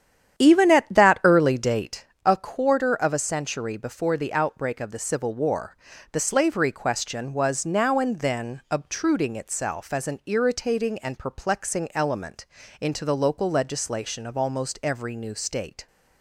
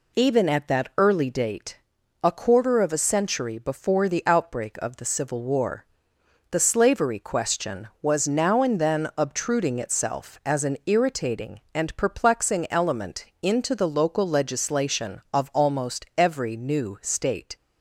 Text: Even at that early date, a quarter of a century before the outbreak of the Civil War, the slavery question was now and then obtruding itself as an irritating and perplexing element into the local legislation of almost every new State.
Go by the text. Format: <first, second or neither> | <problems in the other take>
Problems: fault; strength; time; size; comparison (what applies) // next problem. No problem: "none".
second | starts louder than the rest; strong; until 2.1 s; 9.5 dB // pauses between "element" and "into"; slight; at 12.4 s; 0.34 s long; slight in the second